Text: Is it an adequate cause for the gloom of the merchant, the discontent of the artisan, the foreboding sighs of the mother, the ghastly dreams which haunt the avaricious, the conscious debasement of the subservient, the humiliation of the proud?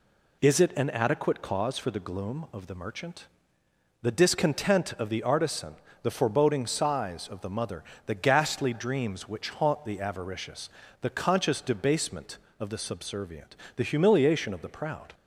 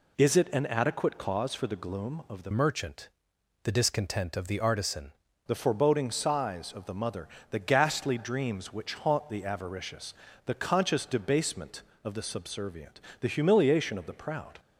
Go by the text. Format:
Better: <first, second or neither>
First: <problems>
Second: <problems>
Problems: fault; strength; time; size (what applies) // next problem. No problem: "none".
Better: first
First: none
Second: changes voice from "merchant" to "artisan"; from 2.5 to 5.1 s; 2.6 s long